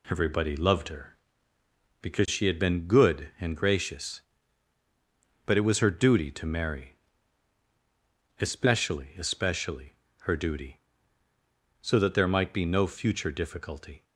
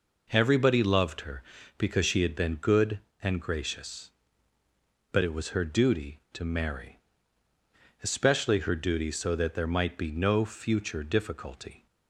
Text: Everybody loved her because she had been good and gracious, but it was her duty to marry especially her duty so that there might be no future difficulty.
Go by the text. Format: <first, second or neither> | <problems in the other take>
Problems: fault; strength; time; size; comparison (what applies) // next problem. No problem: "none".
second | pauses between "marry" and "especially"; strong; at 6.9 s; 1.4 s long; also in the second // says "especially" twice; at 9.1 s